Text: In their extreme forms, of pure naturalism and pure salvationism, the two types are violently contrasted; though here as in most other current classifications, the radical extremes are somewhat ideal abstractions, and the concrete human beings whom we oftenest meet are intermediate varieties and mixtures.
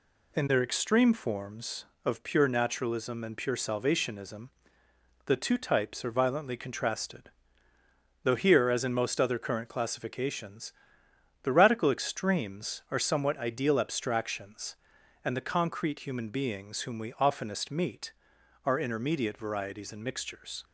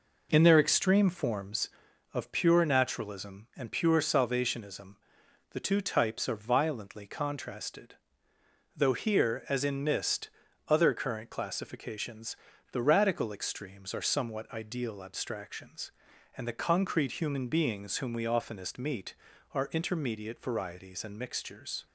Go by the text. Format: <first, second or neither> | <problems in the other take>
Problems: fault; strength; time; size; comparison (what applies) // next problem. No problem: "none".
first | says "mist" for "most"; at 9.8 s